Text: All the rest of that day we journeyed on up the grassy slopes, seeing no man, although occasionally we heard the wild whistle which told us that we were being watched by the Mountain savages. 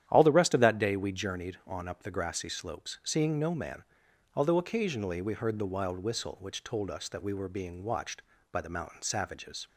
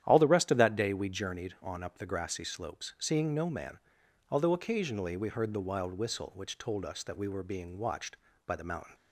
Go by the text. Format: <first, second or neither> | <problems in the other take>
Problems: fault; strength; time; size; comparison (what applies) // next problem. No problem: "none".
first | starts louder than the rest; strong; until 1.0 s; 10.5 dB; strong in the first // stops before "savages"; at 8.9 s